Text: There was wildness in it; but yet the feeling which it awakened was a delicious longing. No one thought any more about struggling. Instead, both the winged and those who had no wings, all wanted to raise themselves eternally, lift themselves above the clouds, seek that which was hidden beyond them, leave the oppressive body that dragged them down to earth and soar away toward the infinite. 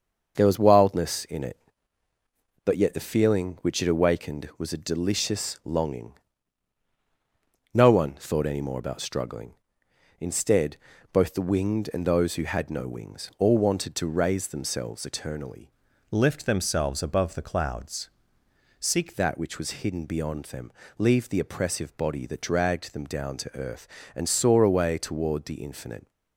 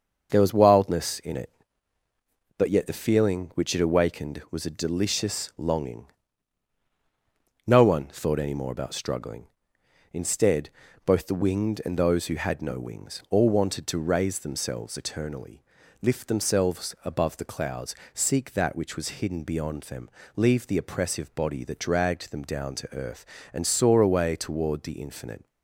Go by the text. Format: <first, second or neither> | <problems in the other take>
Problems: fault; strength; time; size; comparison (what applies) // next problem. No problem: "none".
second | starts louder than the rest; until 1.3 s; 6 dB; also in the second // changes voice from "lift" to "seek"; from 16.1 to 19.1 s; 3.0 s long